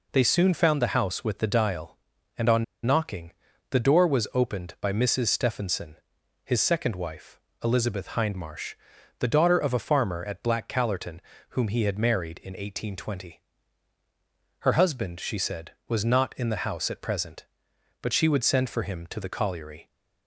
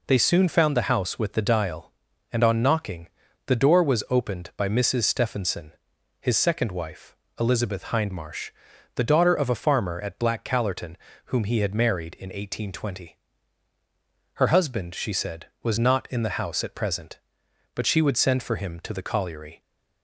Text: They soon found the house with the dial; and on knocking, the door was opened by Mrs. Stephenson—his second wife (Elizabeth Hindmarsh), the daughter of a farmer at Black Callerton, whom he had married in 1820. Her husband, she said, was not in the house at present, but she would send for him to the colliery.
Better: second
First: pauses between "on" and "knocking"; slight; at 2.6 s; 0.21 s long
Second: none

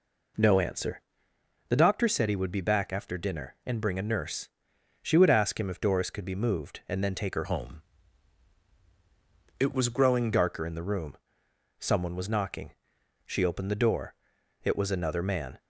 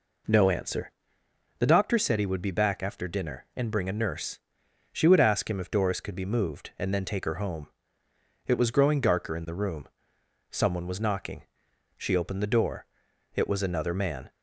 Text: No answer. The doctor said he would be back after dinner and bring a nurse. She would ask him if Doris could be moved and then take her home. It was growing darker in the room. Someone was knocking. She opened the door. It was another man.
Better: second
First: changes voice from "home" to "growing"; from 7.4 to 10.3 s; 2.9 s long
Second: none

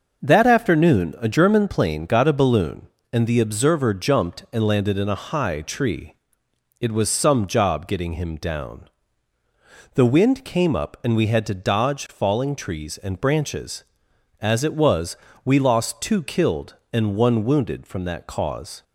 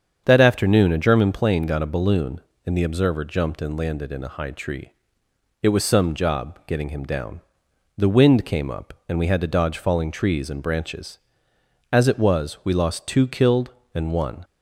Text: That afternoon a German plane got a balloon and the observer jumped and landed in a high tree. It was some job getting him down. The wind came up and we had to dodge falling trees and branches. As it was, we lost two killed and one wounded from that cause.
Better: first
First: starts louder than the rest; noticeable; until 1.2 s; 6 dB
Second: starts louder than the rest; strong; until 1.2 s; 7.5 dB // stops before "wounded from that cause"; at 14.4 s

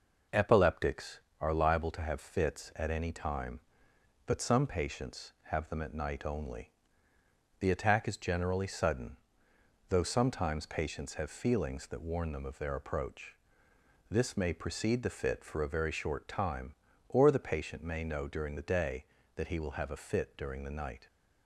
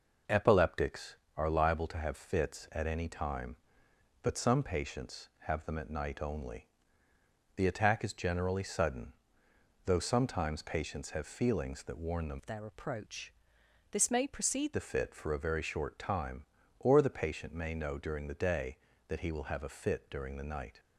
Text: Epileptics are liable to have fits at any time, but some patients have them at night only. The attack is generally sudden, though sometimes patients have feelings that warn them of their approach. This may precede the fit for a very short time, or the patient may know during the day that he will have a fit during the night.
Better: first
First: none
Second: changes voice from "of" to "precede"; from 12.3 to 14.7 s; 2.4 s long

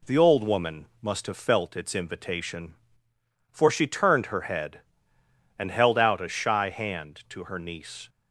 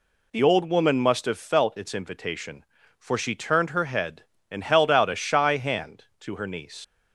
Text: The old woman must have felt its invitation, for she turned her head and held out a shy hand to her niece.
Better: first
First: none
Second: leaves "niece" unfinished; at 6.8 s; 80 ms

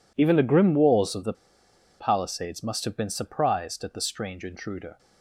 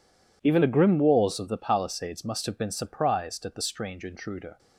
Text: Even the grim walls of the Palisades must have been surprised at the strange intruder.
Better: second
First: pauses between "the" and "Palisades"; noticeable; at 1.3 s; 0.65 s long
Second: none

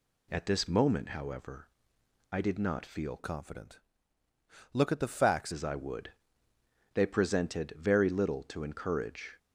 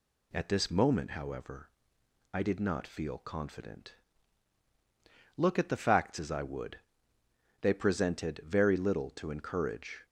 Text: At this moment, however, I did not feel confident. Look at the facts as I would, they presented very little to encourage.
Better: second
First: changes voice from "confident" to "facts"; from 3.1 to 5.5 s; 2.4 s long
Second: none

